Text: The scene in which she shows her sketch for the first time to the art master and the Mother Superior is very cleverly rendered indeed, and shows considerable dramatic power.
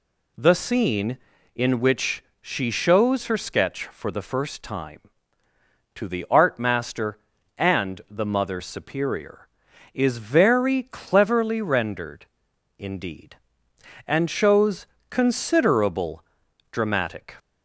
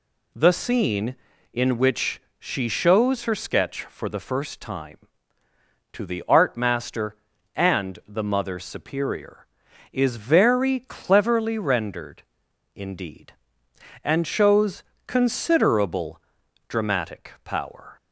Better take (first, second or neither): second